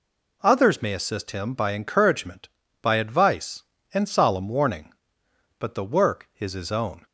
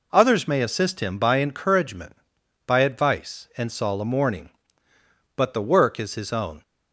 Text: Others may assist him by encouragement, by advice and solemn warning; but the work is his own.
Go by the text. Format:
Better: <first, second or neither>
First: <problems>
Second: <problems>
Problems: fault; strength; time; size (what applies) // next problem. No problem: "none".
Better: neither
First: none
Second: none